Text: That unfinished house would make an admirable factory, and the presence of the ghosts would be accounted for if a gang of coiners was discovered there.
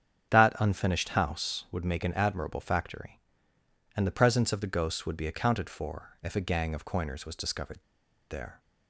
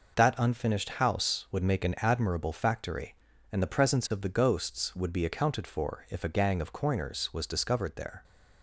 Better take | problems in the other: second | starts louder than the rest; strong; until 1.3 s; 8 dB // pauses between "discovered" and "there"; noticeable; at 7.7 s; 0.51 s long

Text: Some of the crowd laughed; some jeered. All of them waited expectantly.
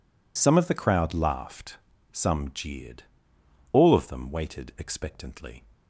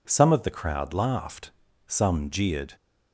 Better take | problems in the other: first | stops before "All of them waited expectantly"; at 2.7 s

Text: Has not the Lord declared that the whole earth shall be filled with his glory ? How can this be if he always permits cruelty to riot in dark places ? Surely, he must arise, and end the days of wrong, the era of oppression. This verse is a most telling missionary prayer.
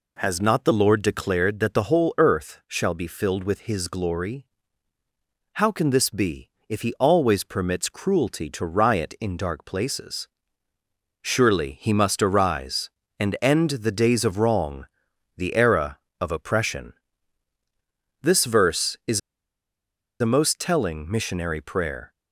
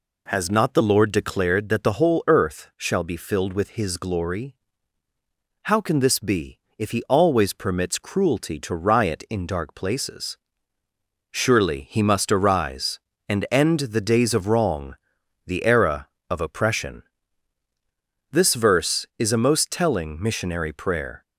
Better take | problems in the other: second | pauses between "be" and "if"; slight; at 6.4 s; 0.18 s long; slight in the second // pauses between "is" and "a"; at 19.1 s; 1.0 s long

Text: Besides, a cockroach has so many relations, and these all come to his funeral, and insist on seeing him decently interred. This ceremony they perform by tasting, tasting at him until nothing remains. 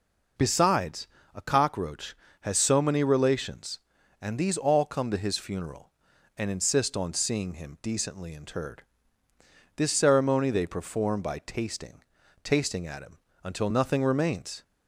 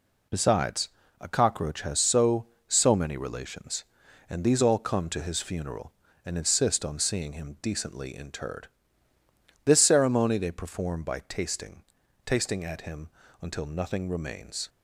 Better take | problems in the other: first | says "so" twice; at 2.6 s // pauses between "him" and "until"; slight; at 13.0 s; 0.32 s long; slight in the first

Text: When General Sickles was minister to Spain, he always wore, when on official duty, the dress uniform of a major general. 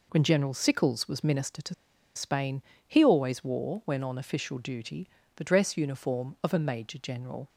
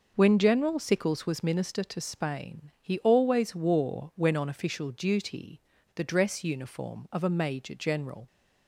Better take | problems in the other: second | pauses between "to" and "Spain"; at 1.7 s; 0.41 s long

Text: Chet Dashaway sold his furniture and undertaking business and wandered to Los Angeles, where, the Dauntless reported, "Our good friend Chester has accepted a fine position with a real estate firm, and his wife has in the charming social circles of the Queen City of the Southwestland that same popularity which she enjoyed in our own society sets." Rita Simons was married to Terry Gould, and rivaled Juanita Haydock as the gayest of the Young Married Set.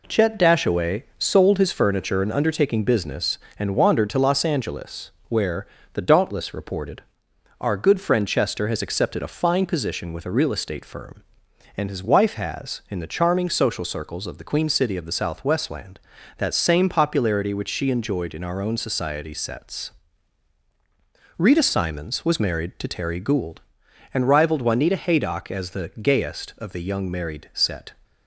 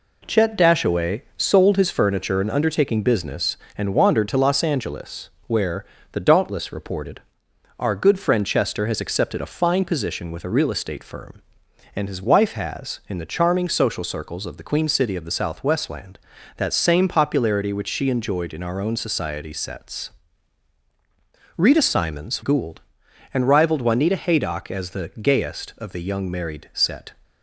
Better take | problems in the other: first | skips "was married to Terry"; at 22.4 s

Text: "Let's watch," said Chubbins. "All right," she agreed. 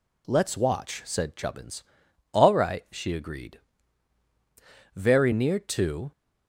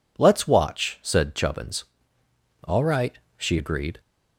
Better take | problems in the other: second | goes on to say "Very near to"; noticeable; from 4.9 s on; 1.1 s long

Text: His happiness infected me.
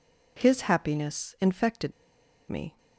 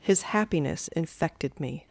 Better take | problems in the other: second | pauses between "infected" and "me"; noticeable; at 1.9 s; 0.58 s long

